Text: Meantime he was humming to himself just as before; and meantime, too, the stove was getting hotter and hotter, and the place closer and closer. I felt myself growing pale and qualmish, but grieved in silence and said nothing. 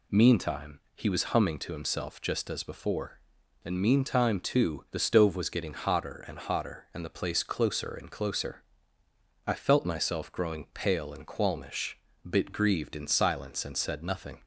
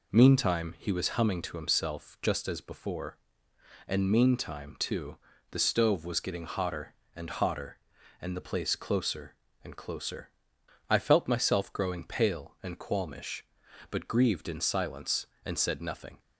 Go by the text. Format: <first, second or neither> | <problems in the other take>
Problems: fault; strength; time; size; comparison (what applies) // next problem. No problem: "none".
second | pauses between "Meantime" and "he"; slight; at 0.7 s; 0.16 s long // says "bit" for "but"; at 12.2 s